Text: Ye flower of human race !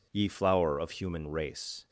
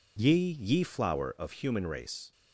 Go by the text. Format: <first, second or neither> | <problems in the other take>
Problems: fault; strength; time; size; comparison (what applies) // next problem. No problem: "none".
first | says "Ye" twice; at 0.5 s